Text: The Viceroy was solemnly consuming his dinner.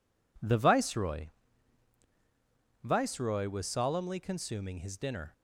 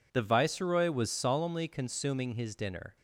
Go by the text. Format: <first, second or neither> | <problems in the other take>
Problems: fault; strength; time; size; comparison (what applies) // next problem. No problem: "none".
second | says "Viceroy" twice; at 2.8 s